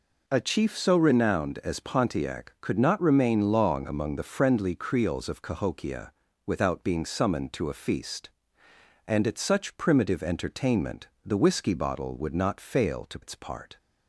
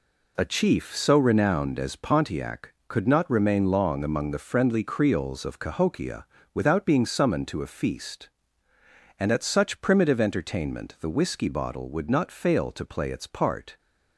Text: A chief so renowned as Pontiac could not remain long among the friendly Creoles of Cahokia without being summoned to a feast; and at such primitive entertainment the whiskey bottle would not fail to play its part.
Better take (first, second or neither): second